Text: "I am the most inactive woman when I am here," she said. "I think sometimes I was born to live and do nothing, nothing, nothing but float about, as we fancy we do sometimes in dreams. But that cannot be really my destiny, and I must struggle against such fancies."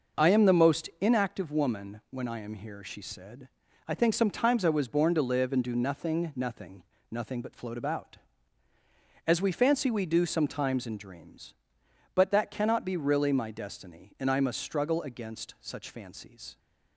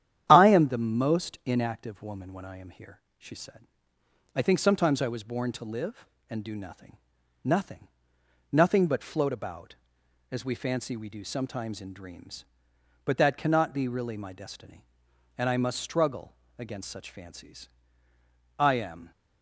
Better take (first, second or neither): first